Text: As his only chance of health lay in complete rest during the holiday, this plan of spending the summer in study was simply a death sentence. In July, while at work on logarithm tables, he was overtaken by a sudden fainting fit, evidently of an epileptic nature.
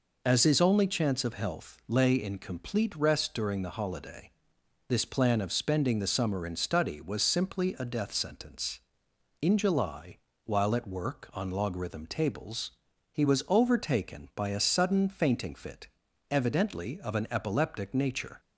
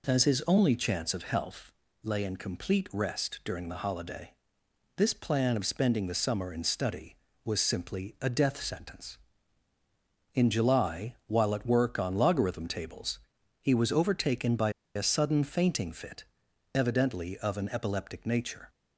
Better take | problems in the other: first | pauses between "health" and "lay"; slight; at 1.7 s; 0.30 s long // pauses between "by" and "a"; slight; at 14.7 s; 0.24 s long

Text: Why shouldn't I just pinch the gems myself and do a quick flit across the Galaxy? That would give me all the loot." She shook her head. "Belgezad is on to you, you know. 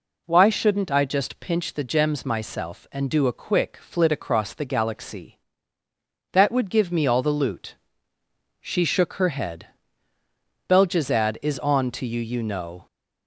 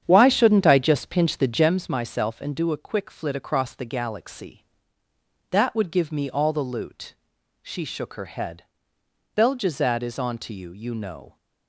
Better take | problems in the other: first | starts louder than the rest; strong; until 1.8 s; 9 dB

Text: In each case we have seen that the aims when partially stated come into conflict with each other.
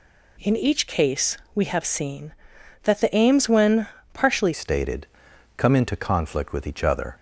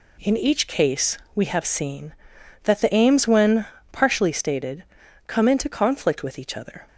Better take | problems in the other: second | pauses between "case" and "we"; slight; at 1.3 s; 0.20 s long; slight in the second // pauses between "when" and "partially"; slight; at 3.8 s; 0.24 s long; slight in the second // changes voice at "stated"; from 4.5 s on; 2.6 s long // pauses between "stated" and "come"; noticeable; at 5.0 s; 0.48 s long; also in the second

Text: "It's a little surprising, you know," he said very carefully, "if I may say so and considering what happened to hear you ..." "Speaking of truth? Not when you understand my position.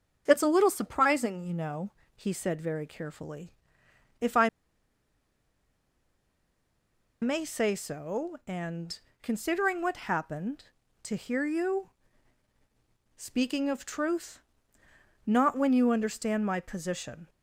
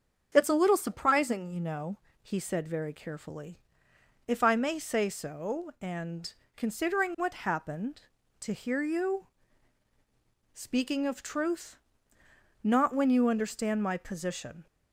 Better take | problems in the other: second | starts louder than the rest; strong; until 1.2 s; 7.5 dB; strong in the second // pauses between "I" and "may"; strong; at 4.4 s; 2.7 s long // pauses between "and" and "considering"; slight; at 8.9 s; 0.24 s long; slight in the second

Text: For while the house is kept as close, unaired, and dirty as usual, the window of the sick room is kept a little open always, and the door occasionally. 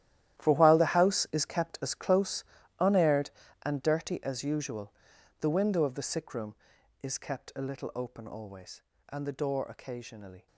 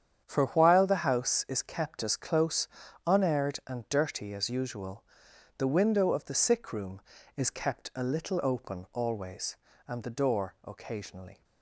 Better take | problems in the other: second | gets quieter; strong; throughout; 15.5 dB // starts louder than the rest; strong; until 1.4 s; 12.5 dB; strong in the second

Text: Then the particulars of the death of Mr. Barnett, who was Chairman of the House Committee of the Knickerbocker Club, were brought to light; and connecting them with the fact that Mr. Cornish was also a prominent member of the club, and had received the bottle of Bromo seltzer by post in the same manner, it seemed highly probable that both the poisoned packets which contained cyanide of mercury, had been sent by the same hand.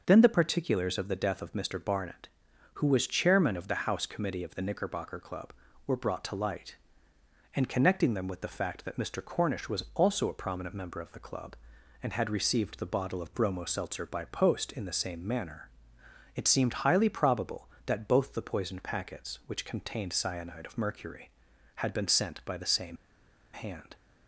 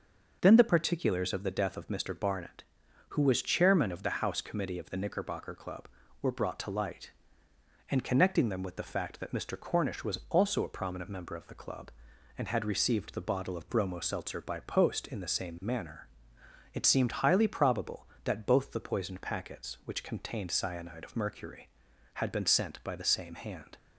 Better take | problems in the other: second | starts louder than the rest; noticeable; until 1.0 s; 6 dB; noticeable in the second // pauses between "same" and "hand"; noticeable; at 22.9 s; 0.56 s long

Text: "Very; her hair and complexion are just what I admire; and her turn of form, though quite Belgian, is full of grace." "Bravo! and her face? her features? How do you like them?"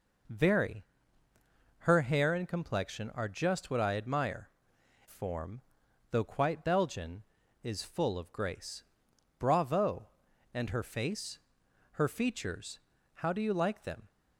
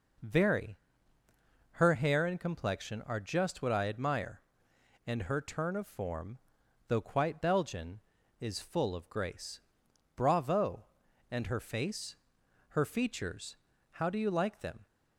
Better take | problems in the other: second | skips "and her turn of"; at 4.7 s

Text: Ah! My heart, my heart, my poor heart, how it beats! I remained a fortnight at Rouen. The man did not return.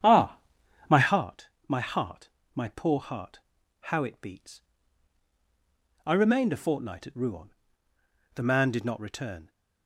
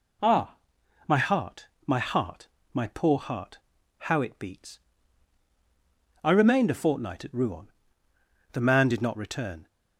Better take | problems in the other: second | starts louder than the rest; strong; until 1.3 s; 9 dB

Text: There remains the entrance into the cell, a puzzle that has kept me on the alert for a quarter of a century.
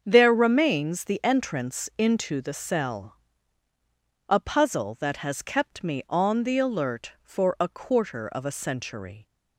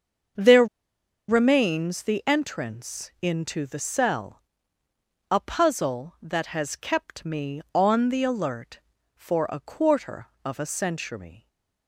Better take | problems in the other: first | starts louder than the rest; until 2.0 s; 7 dB; also in the first // pauses between "There" and "remains"; noticeable; at 0.6 s; 0.63 s long // stays silent after the last word; slight; from 11.3 s on; 0.5 s long

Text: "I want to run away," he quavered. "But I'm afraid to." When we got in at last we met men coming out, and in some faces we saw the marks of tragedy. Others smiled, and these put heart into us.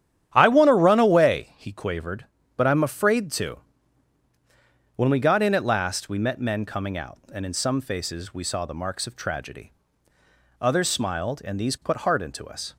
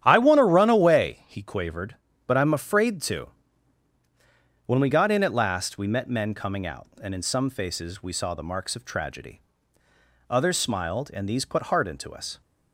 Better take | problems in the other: neither | starts louder than the rest; strong; the same in both

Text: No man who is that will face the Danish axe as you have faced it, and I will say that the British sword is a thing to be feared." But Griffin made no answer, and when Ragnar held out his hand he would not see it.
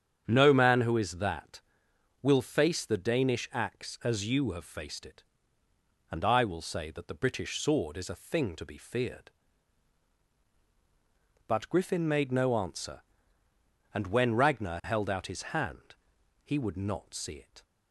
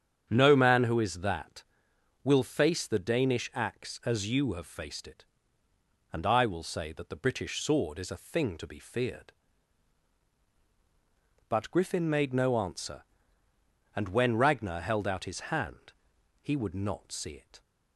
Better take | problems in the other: neither | starts louder than the rest; strong; the same in both // pauses between "hand" and "he"; noticeable; the same in both

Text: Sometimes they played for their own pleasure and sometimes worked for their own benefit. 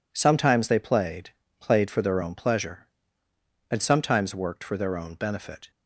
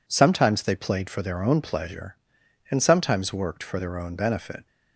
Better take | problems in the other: second | says "played" twice; at 1.5 s

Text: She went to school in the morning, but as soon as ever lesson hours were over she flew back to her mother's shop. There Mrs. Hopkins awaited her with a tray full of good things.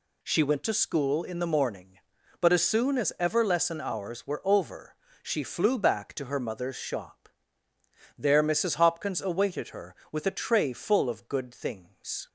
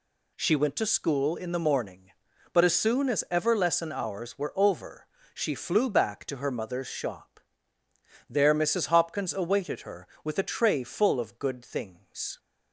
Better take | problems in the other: neither | pauses between "over" and "she"; slight; the same in both

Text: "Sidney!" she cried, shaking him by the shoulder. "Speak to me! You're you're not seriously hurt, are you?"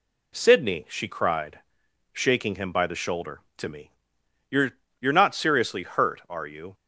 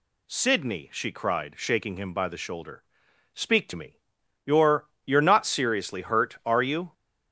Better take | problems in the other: second | skips "Speak"; at 3.5 s // pauses between "You're" and "you're"; slight; at 4.7 s; 0.28 s long; slight in the second

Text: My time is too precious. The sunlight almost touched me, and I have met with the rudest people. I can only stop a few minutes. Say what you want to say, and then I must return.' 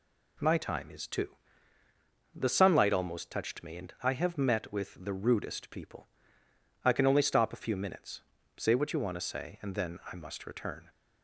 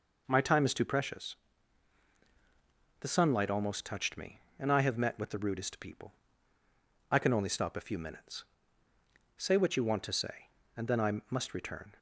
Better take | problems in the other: second | skips "precious"; at 1.8 s

